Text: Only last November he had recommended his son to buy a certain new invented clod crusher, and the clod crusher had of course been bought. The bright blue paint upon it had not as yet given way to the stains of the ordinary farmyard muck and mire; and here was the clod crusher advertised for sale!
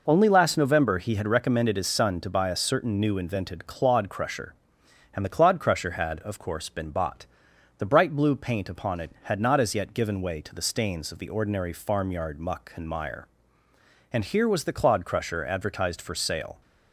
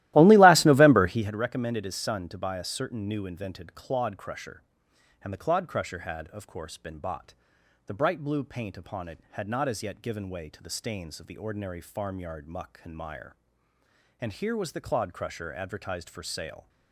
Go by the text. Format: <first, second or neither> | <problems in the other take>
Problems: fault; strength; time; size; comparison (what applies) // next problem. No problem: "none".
first | starts louder than the rest; strong; until 1.4 s; 16 dB